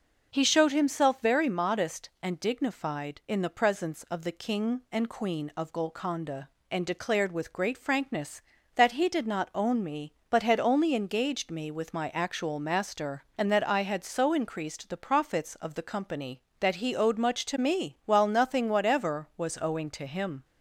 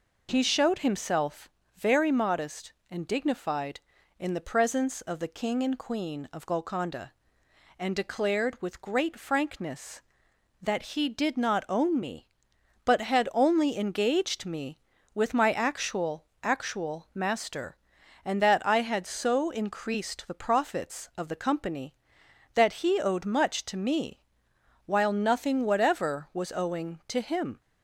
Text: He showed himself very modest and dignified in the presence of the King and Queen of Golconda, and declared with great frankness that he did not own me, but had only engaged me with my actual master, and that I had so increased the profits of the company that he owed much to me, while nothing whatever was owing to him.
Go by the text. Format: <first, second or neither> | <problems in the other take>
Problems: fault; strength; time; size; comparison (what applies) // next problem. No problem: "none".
first | pauses between "himself" and "very"; slight; at 1.4 s; 0.24 s long // says "actual" twice; at 16.4 s